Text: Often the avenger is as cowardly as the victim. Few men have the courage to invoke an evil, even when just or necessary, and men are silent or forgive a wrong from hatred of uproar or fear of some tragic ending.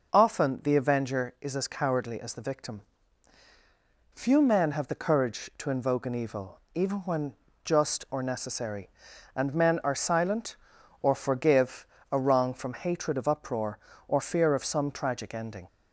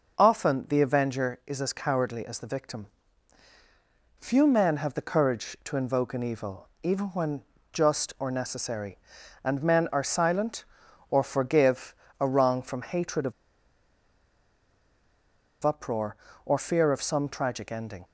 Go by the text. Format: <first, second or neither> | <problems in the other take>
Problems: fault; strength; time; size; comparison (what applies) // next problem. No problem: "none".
first | pauses between "when" and "just"; slight; at 7.4 s; 0.32 s long; slight in the first // pauses between "forgive" and "a"; slight; at 11.9 s; 0.24 s long; slight in the first // pauses between "of" and "uproar"; strong; at 13.3 s; 2.3 s long